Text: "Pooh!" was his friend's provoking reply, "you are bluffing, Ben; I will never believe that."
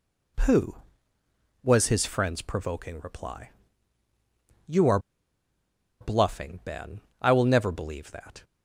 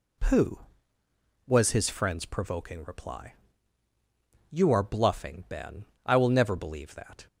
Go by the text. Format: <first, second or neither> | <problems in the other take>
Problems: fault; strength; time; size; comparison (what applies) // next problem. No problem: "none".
second | pauses between "are" and "bluffing"; at 4.9 s; 1.0 s long